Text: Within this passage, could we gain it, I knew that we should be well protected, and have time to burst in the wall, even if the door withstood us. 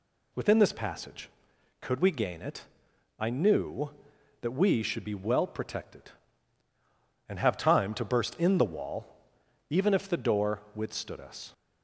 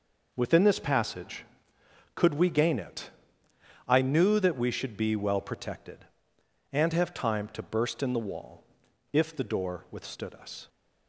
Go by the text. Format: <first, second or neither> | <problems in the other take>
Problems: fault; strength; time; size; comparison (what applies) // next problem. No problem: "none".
first | skips "even"; at 8.8 s